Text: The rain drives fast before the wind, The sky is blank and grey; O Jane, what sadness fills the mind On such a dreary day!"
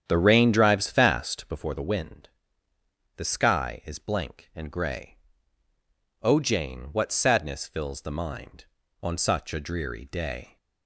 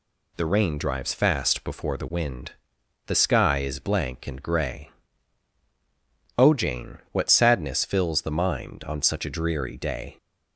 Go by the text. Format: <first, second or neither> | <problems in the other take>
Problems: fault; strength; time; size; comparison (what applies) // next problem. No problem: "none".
second | starts louder than the rest; strong; until 1.6 s; 9 dB